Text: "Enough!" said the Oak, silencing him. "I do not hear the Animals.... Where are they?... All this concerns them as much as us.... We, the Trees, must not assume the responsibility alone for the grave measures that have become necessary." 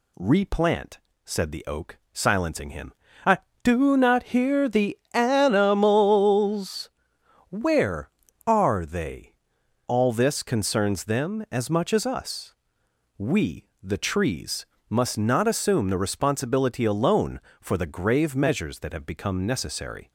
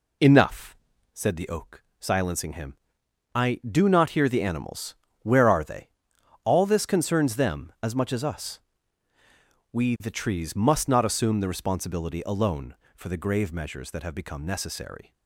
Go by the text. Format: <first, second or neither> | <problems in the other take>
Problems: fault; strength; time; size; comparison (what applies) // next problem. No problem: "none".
second | says "Replant" for "Enough"; at 0.1 s // pauses between "the" and "Animals"; slight; at 4.9 s; 0.16 s long